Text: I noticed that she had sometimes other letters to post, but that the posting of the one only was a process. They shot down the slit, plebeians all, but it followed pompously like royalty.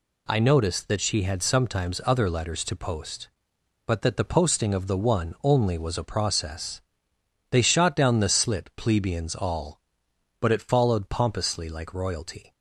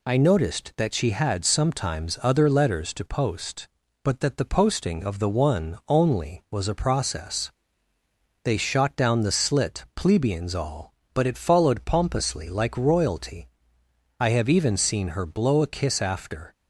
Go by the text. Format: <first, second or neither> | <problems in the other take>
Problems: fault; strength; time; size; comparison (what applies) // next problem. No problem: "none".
first | goes on to say "I have even seen her blow a kiss after"; strong; from 14.1 s on; 2.3 s long